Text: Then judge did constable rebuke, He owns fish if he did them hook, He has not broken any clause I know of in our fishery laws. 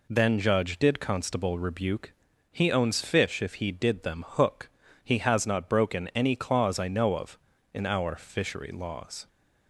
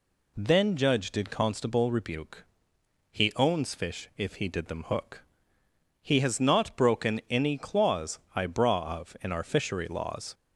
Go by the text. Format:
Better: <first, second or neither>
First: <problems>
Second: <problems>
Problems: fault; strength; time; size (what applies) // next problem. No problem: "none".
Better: first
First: none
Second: pauses between "clause" and "I"; slight; at 8.1 s; 0.16 s long // says "braw" for "know"; at 8.4 s